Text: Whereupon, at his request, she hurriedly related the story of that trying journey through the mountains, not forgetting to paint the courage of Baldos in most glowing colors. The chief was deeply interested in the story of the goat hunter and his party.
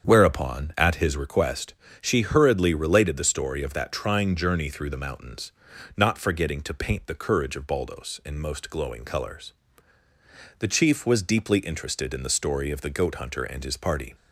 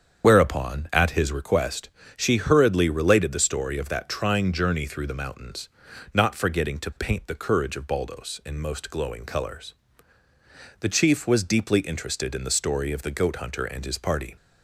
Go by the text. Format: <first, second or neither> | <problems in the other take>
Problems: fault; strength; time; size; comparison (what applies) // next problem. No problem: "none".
first | loses the start of "Whereupon"; at 0.2 s; 55 ms // starts louder than the rest; strong; until 1.3 s; 7.5 dB; strong in the first